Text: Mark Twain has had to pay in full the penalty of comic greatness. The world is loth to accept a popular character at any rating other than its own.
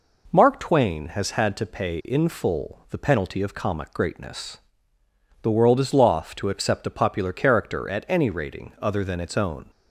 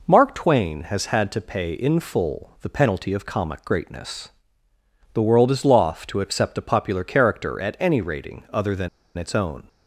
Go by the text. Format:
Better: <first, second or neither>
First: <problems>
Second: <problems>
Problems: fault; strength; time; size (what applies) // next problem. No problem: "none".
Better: first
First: none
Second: pauses between "than" and "its"; slight; at 8.8 s; 0.29 s long